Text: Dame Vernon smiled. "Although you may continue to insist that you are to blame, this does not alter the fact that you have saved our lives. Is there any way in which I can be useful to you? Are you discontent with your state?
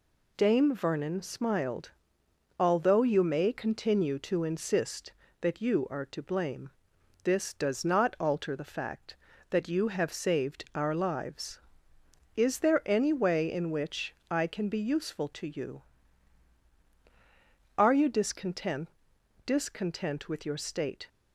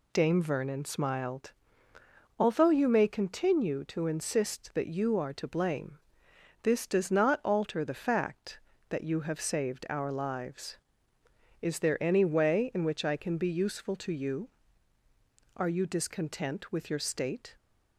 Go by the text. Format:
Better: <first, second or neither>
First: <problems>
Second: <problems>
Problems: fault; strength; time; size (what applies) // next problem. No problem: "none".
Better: second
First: pauses between "which" and "I"; slight; at 14.1 s; 0.16 s long // says "discontent" twice; at 19.4 s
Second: none